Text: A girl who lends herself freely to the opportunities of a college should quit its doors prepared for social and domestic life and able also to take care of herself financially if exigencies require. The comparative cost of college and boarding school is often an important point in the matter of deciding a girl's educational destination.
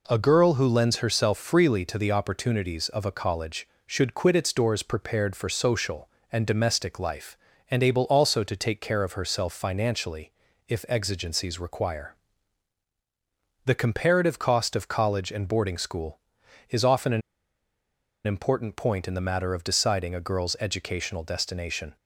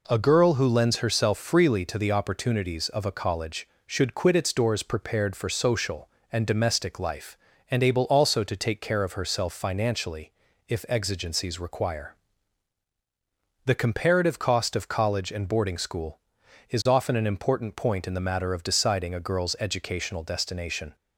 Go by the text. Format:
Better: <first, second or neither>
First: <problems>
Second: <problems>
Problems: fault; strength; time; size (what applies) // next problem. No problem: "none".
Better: second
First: pauses between "financially" and "if"; at 10.2 s; 0.38 s long // pauses between "an" and "important"; at 17.2 s; 1.0 s long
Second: pauses between "financially" and "if"; at 10.2 s; 0.38 s long